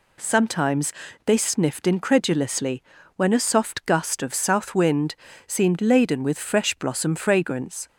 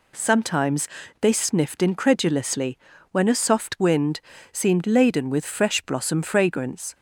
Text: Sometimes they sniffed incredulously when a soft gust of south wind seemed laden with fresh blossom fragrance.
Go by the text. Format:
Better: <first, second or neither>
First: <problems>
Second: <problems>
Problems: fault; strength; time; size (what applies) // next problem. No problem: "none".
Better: first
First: pauses between "Sometimes" and "they"; slight; at 0.9 s; 0.34 s long // pauses between "incredulously" and "when"; slight; at 2.8 s; 0.32 s long // pauses between "wind" and "seemed"; slight; at 5.1 s; 0.32 s long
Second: pauses between "Sometimes" and "they"; slight; at 0.8 s; 0.34 s long // pauses between "incredulously" and "when"; slight; at 2.7 s; 0.32 s long // skips "gust of south"; at 3.8 s // pauses between "wind" and "seemed"; slight; at 4.2 s; 0.32 s long